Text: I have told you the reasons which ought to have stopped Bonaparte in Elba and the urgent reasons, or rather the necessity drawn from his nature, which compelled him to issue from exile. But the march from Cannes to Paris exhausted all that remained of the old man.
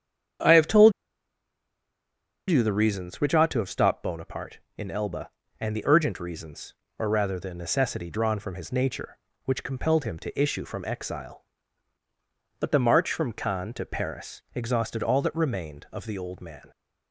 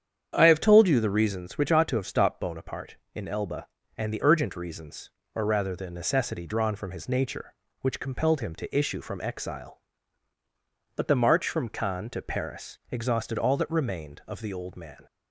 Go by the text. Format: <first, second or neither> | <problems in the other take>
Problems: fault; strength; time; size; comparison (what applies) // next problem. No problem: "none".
second | starts louder than the rest; strong; until 3.0 s; 8.5 dB; strong in the second // pauses between "told" and "you"; strong; at 0.9 s; 1.5 s long